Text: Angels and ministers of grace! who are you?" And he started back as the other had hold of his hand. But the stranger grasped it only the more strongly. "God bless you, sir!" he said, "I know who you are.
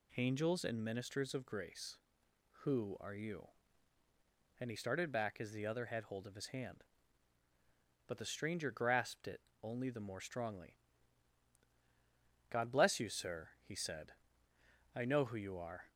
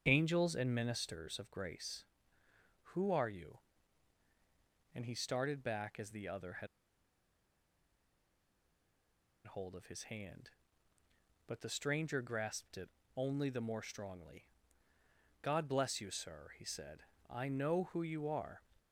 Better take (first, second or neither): first